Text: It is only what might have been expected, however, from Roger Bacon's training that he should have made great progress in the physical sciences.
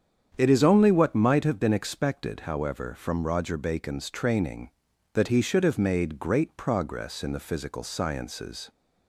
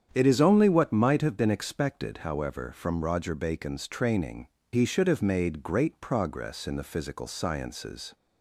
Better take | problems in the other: first | starts louder than the rest; strong; until 1.1 s; 8.5 dB; strong in the first // skips "that"; at 4.6 s

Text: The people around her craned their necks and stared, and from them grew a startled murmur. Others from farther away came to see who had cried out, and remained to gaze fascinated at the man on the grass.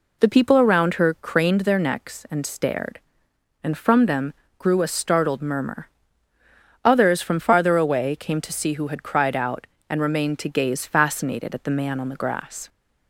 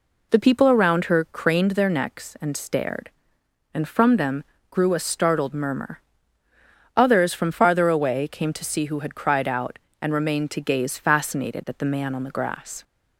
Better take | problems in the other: neither | pauses between "them" and "grew"; slight; the same in both

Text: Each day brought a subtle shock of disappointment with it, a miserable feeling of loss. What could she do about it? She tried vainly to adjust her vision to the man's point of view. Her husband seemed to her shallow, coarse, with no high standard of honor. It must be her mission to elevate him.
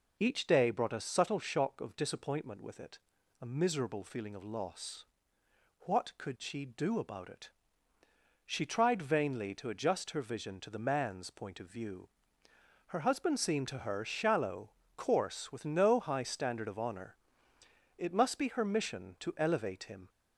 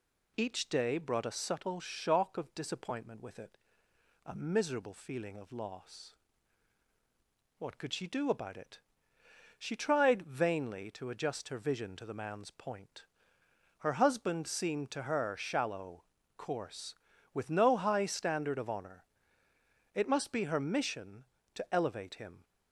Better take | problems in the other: first | skips "of view"; at 13.4 s

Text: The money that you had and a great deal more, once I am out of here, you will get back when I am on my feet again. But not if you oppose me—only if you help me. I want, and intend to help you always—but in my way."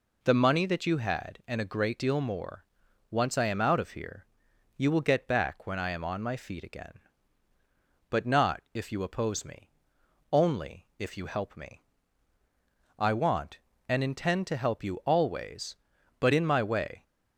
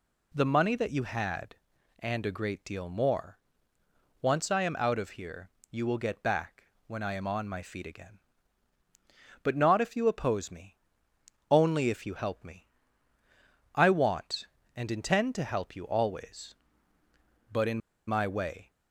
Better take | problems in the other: first | pauses between "back" and "when"; slight; at 6.6 s; 0.24 s long // pauses between "in" and "my"; slight; at 17.7 s; 0.28 s long

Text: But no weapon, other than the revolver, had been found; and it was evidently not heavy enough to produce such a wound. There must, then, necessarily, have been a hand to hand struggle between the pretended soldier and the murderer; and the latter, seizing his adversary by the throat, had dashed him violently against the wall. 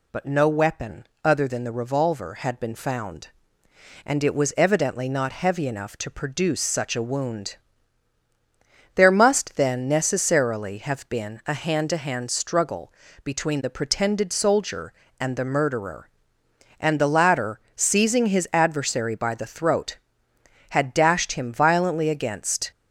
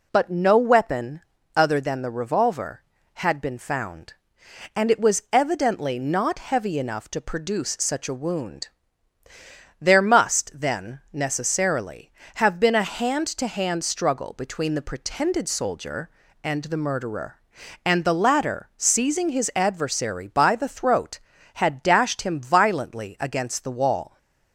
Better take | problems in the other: second | pauses between "struggle" and "between"; slight; at 12.9 s; 0.32 s long // stops before "the wall"; at 22.7 s

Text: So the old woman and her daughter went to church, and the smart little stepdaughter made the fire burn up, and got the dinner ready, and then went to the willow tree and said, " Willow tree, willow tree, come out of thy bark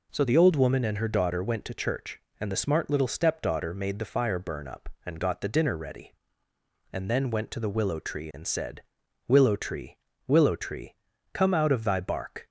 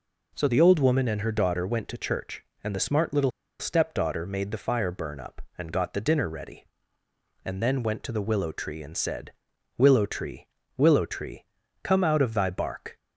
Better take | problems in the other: first | pauses between "little" and "stepdaughter"; slight; at 3.2 s; 0.29 s long

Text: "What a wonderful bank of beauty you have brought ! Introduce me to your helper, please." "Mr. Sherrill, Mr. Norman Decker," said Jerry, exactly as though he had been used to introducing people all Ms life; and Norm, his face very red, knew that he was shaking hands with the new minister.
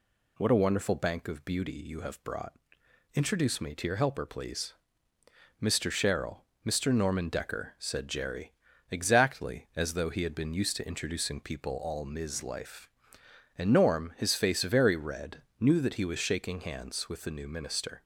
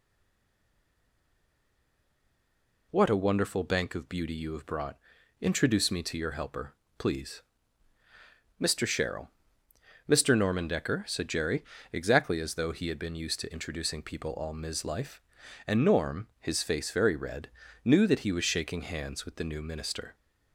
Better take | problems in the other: first | stays silent before the first word; strong; until 2.9 s; 2.9 s long

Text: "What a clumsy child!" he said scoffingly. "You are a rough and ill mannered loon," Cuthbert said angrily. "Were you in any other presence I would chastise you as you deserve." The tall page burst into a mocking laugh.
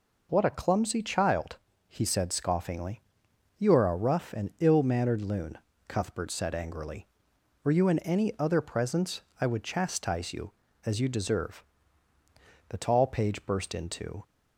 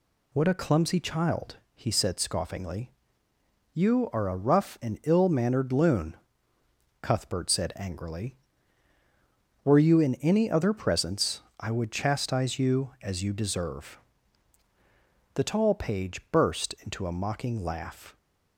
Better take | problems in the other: second | pauses between "presence" and "I"; slight; at 9.2 s; 0.18 s long; slight in the second // stops before "a mocking laugh"; at 14.2 s

